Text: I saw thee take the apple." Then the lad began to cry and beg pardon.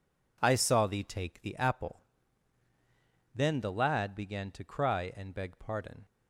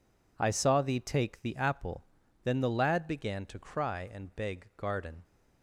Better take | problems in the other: first | says "garden" for "pardon"; at 4.7 s

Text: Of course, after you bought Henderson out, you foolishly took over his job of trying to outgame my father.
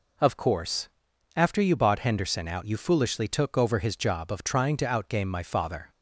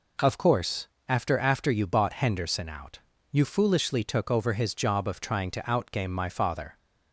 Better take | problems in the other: first | says "after" twice; at 1.3 s

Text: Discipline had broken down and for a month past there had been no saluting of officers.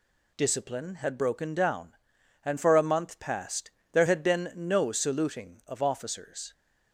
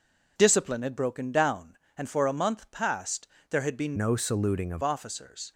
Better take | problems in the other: first | pauses between "past" and "there"; slight; at 3.2 s; 0.24 s long; slight in the first // changes voice from "no" to "of"; from 3.9 to 4.8 s; 0.9 s long

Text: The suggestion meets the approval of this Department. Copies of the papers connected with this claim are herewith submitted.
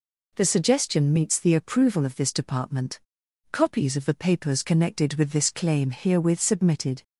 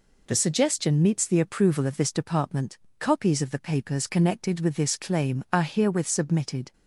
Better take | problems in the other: second | skips "are"; at 5.9 s

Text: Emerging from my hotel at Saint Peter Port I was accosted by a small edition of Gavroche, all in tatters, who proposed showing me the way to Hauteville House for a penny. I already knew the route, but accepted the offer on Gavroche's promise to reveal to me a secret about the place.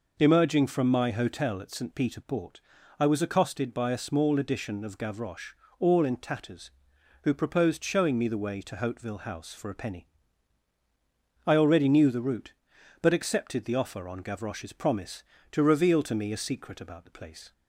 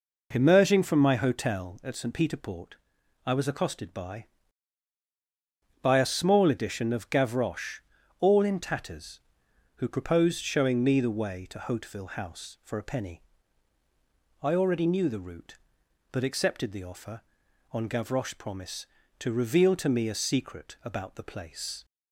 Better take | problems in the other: first | pauses between "Port" and "I"; noticeable; at 2.7 s; 0.50 s long; also in the first // says "by" twice; at 5.8 s

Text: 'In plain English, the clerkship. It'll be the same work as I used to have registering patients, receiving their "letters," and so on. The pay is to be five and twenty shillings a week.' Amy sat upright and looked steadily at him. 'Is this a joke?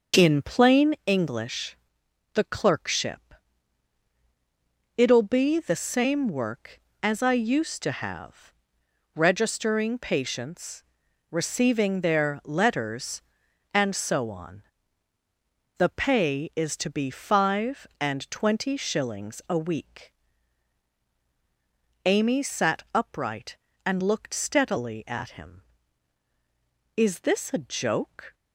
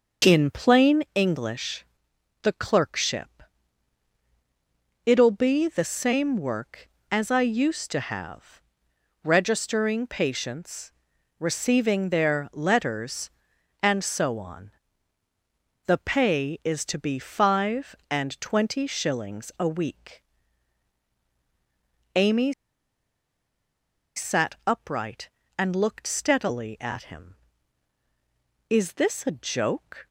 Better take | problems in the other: first | starts louder than the rest; noticeable; until 1.3 s; 6 dB // pauses between "have" and "registering"; noticeable; at 8.6 s; 0.64 s long; noticeable in the first // pauses between "Amy" and "sat"; strong; at 22.5 s; 1.6 s long

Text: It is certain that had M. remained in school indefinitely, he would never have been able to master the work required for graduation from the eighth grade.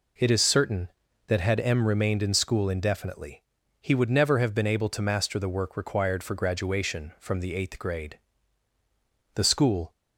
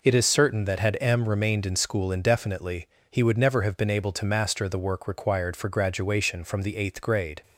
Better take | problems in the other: second | goes on to say "The school"; from 9.3 s on; 0.58 s long

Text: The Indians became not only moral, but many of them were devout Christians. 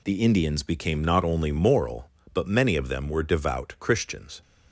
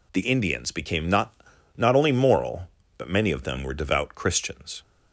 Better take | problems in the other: first | says "not" twice; at 1.7 s

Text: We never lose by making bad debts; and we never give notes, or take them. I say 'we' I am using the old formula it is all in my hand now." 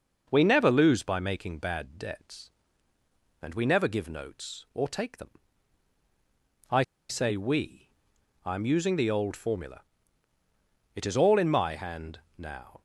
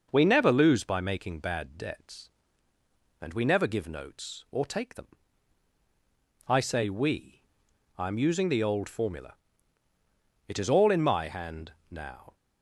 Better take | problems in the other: second | pauses between "I" and "say"; slight; at 6.8 s; 0.26 s long // pauses between "we" and "I"; noticeable; at 7.8 s; 0.56 s long; noticeable in the second // pauses between "formula" and "it"; at 9.7 s; 1.1 s long; also in the second // pauses between "hand" and "now"; slight; at 12.1 s; 0.16 s long; slight in the second

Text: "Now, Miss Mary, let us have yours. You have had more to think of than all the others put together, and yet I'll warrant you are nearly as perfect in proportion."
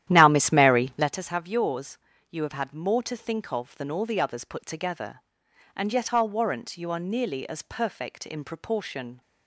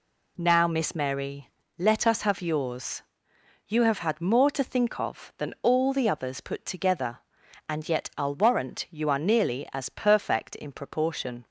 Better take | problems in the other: second | starts louder than the rest; strong; until 1.2 s; 12 dB

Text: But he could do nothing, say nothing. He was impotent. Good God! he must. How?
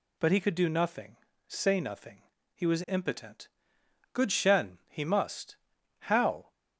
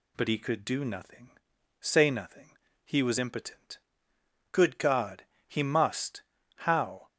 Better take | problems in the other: second | says "Shen" for "God"; at 4.3 s

